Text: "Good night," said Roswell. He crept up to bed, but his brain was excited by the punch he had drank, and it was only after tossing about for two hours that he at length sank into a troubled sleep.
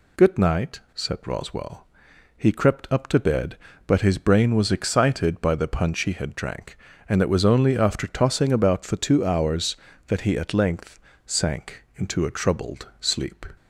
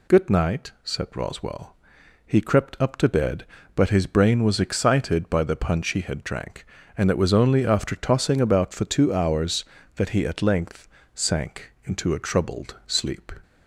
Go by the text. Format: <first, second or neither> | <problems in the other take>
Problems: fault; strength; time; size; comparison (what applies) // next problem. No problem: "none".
neither | pauses between "length" and "sank"; slight; the same in both